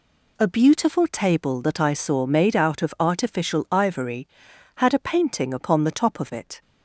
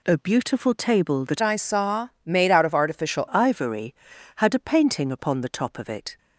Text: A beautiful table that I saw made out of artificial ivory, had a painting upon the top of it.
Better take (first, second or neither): first